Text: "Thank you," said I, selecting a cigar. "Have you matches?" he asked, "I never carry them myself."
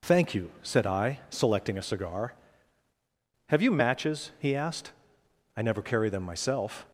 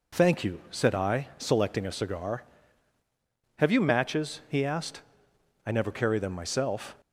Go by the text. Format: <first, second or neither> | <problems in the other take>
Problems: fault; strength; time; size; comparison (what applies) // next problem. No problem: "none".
neither | none